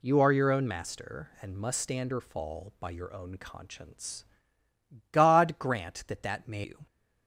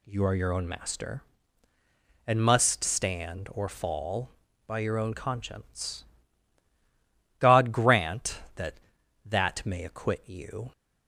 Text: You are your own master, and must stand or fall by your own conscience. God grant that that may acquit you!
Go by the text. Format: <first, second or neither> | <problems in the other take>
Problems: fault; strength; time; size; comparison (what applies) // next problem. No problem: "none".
second | skips "acquit"; at 6.6 s